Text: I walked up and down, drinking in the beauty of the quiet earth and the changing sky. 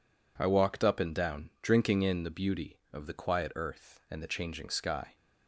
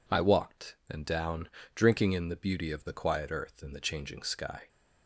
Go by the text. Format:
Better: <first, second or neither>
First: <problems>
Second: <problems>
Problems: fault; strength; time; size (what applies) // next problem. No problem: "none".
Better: first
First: none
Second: skips "up"; at 0.8 s